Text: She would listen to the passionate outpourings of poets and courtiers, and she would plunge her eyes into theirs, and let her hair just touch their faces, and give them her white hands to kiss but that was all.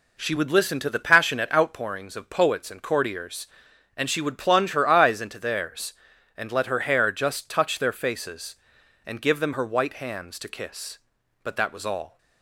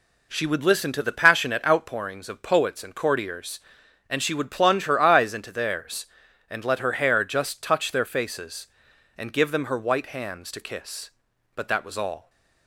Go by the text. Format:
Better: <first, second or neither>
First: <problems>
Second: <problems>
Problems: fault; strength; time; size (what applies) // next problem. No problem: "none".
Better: neither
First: none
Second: none